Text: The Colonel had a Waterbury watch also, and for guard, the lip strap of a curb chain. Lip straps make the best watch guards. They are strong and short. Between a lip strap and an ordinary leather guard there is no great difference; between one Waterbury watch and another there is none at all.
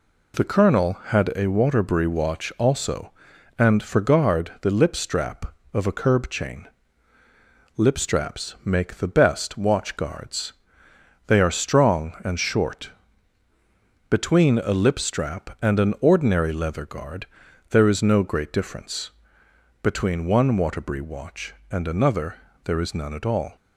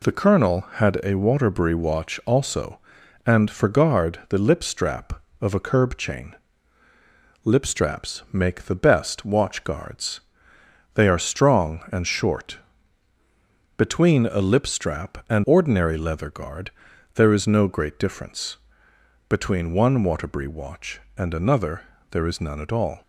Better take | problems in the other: first | skips "an"; at 15.4 s // pauses between "guard" and "there"; at 16.7 s; 0.42 s long; also in the first // pauses between "another" and "there"; slight; at 21.8 s; 0.24 s long; slight in the first

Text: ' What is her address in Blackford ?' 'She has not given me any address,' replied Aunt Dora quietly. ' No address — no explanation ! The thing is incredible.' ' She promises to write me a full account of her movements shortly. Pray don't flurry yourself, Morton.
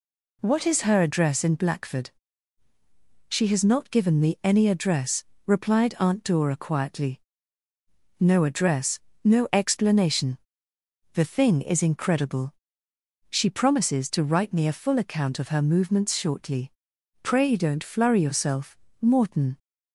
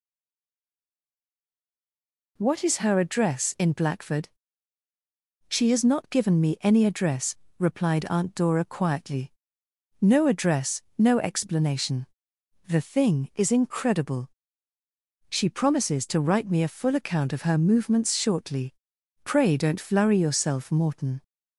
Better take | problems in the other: first | stays silent before the first word; until 2.3 s; 2.3 s long

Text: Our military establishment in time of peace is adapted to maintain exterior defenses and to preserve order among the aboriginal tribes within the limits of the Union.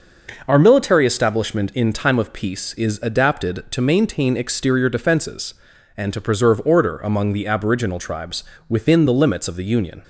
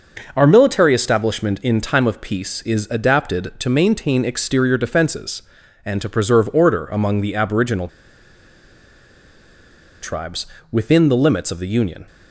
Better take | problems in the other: first | pauses between "aboriginal" and "tribes"; strong; at 7.8 s; 2.1 s long // pauses between "tribes" and "within"; slight; at 10.4 s; 0.24 s long; slight in the first

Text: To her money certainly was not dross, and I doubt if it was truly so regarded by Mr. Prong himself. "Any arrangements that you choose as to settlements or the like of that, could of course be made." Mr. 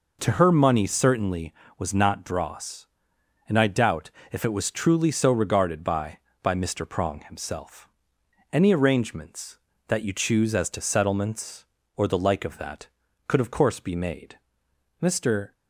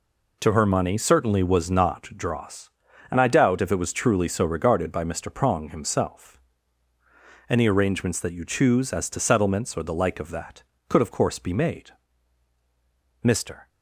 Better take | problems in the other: second | pauses between "doubt" and "if"; slight; at 4.0 s; 0.22 s long // says "by" twice; at 6.4 s

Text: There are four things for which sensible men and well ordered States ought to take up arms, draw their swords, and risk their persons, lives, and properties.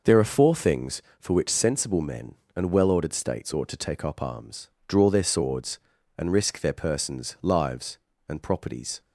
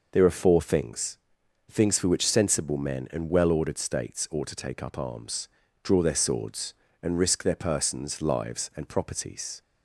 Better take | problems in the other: first | says "things" twice; at 1.7 s

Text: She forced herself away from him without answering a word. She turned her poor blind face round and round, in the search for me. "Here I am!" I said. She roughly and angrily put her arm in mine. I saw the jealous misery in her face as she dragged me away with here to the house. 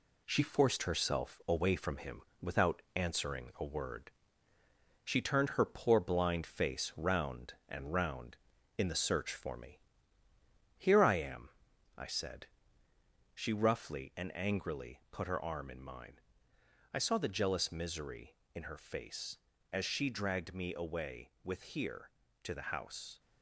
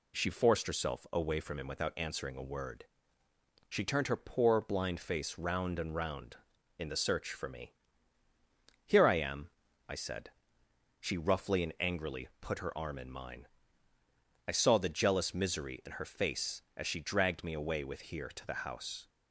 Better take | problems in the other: second | gets quieter; noticeable; throughout; 5 dB // pauses between "him" and "without"; slight; at 2.2 s; 0.20 s long

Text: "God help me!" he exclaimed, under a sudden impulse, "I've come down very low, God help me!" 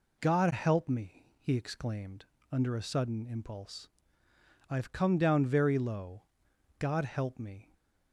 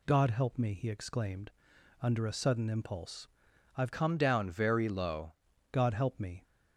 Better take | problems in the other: first | changes voice from "come" to "low"; from 3.9 to 5.3 s; 1.4 s long

